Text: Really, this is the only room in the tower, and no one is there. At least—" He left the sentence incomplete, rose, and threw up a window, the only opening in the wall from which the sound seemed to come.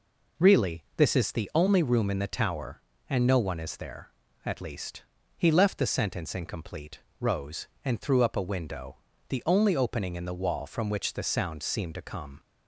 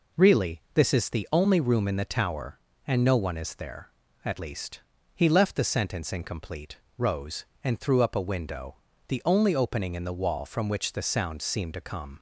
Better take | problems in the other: neither | none

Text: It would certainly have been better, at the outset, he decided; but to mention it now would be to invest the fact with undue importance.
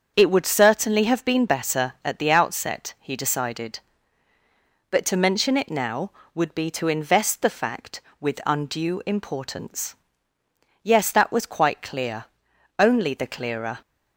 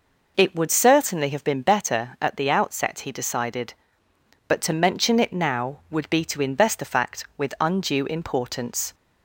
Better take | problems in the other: second | starts louder than the rest; until 1.1 s; 7 dB // goes on to say "Yes that was quite clear only the clearer"; strong; from 10.8 s on; 2.9 s long

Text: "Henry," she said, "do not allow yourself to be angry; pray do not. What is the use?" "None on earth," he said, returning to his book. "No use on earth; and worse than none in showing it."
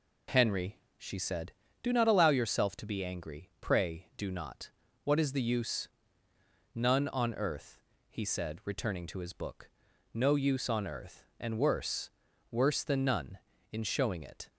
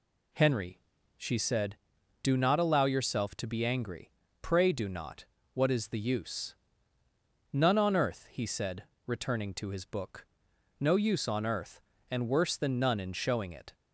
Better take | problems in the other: second | says "worse" twice; at 12.5 s

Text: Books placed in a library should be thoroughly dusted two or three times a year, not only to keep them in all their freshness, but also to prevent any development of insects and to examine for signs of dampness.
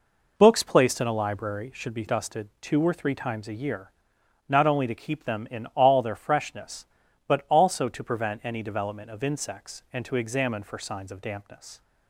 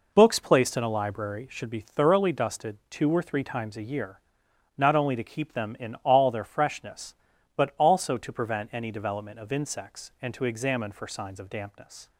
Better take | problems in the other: second | skips "thoroughly"; at 2.0 s

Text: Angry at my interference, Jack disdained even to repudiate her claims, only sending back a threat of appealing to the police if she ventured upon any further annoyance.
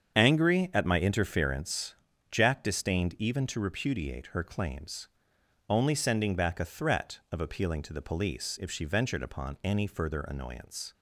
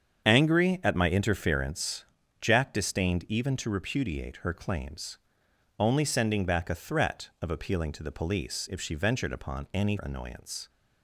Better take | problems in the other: first | starts louder than the rest; strong; until 1.3 s; 7.5 dB; strong in the first // skips "further"; at 9.9 s

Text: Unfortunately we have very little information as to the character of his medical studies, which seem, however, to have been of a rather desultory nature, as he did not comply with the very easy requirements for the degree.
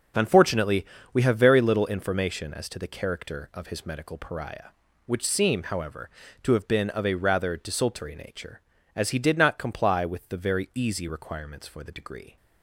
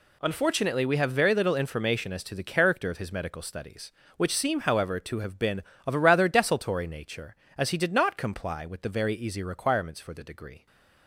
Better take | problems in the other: second | pauses between "Unfortunately" and "we"; slight; at 0.8 s; 0.28 s long // says "pariah" for "studies"; at 4.1 s

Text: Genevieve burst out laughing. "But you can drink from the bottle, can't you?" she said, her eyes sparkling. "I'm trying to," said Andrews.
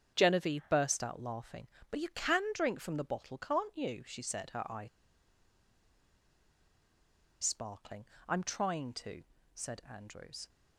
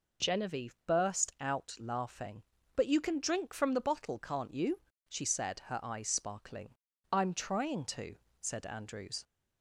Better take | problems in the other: second | starts louder than the rest; strong; until 1.1 s; 8 dB // pauses between "eyes" and "sparkling"; strong; at 4.8 s; 2.5 s long

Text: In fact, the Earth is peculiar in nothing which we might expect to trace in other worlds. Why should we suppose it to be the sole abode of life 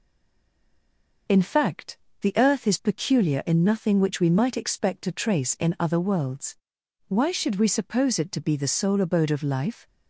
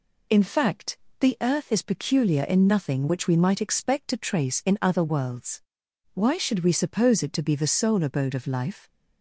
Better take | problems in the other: second | stays silent before the first word; noticeable; until 1.2 s; 1.2 s long

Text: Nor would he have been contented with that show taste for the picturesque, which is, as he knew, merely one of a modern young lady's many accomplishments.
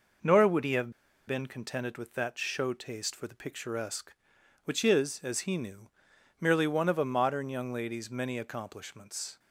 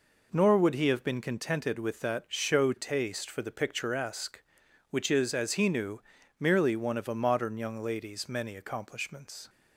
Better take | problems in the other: second | pauses between "have" and "been"; slight; at 0.9 s; 0.35 s long

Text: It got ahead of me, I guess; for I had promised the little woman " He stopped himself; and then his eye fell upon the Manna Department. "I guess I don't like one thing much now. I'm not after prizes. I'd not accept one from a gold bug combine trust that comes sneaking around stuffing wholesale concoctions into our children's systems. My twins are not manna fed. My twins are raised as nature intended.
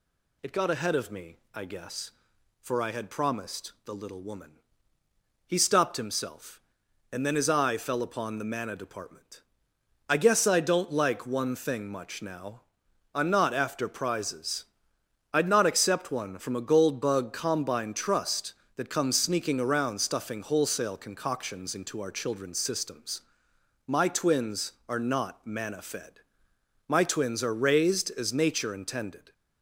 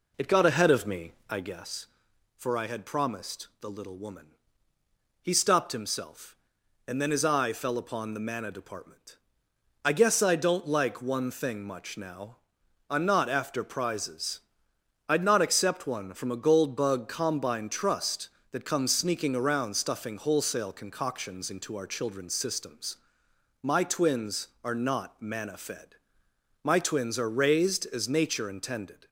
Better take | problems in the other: first | starts louder than the rest; noticeable; until 1.6 s; 4 dB

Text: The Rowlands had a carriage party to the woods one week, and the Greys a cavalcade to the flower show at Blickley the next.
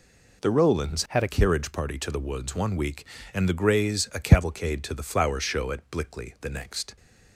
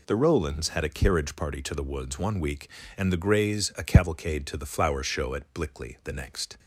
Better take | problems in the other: second | changes voice from "had" to "a"; from 1.0 to 1.2 s; 0.2 s long

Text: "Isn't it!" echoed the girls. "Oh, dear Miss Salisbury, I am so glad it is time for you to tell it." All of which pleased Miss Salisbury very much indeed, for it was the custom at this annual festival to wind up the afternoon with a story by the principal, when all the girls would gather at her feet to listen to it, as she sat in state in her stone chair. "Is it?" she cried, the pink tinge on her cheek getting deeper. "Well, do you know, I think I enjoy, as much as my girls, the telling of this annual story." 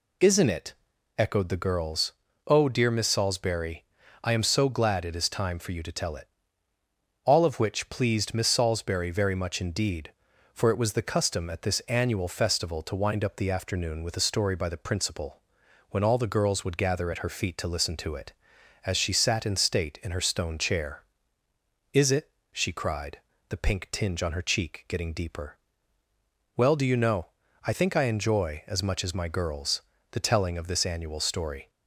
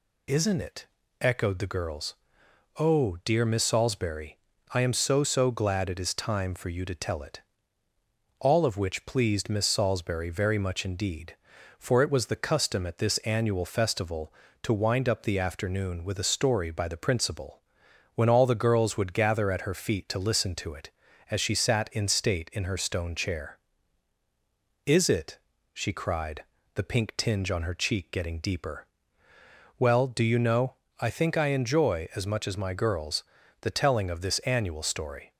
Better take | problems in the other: first | says "so" twice; at 5.2 s

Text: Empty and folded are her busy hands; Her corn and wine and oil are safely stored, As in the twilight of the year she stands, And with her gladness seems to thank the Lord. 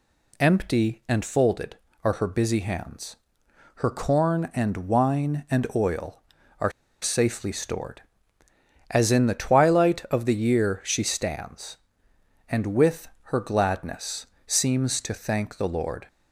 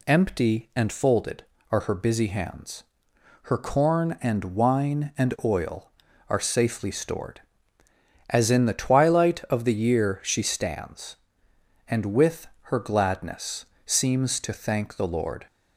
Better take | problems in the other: second | pauses between "are" and "safely"; slight; at 6.7 s; 0.30 s long // pauses between "with" and "her"; slight; at 13.0 s; 0.16 s long; slight in the second // pauses between "gladness" and "seems"; slight; at 14.2 s; 0.20 s long; slight in the second

